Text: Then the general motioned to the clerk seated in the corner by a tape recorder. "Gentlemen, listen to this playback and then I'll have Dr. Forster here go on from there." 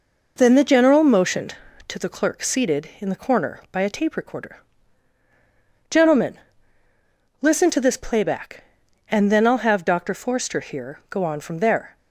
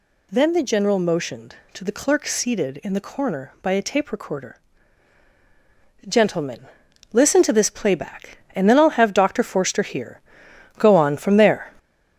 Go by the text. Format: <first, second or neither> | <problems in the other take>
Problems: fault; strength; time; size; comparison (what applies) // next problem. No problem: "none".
first | gets louder; noticeable; throughout; 4.5 dB // pauses between "here" and "go"; noticeable; at 10.2 s; 0.58 s long